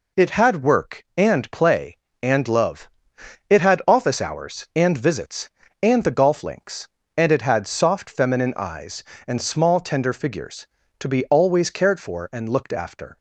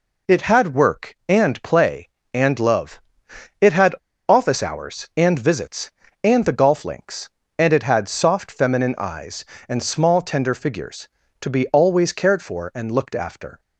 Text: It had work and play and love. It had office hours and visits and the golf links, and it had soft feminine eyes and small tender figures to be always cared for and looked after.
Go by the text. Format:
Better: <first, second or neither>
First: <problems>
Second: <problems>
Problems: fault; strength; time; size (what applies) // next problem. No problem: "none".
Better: first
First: none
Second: pauses between "had" and "office"; slight; at 3.9 s; 0.36 s long